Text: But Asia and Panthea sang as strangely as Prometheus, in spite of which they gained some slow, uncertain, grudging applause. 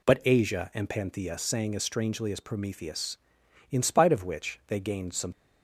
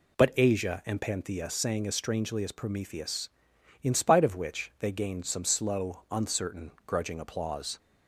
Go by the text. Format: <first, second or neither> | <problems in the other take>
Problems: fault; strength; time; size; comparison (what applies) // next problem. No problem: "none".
second | stops before "slow uncertain grudging applause"; at 5.3 s